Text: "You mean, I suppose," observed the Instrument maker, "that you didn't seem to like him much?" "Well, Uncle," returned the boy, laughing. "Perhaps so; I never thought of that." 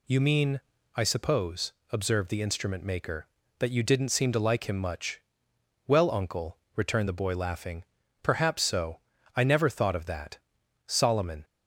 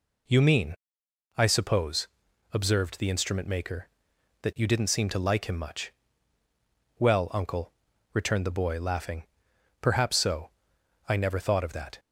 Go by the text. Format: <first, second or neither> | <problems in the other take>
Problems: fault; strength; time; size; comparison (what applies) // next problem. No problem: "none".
second | goes on to say "Solomon"; from 10.8 s on; 0.58 s long